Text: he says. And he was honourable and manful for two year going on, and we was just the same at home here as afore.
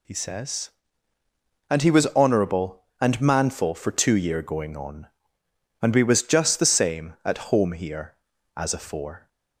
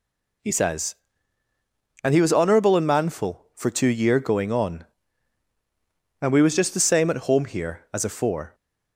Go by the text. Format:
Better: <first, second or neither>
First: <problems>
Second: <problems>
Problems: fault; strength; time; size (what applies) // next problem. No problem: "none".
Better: neither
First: none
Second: none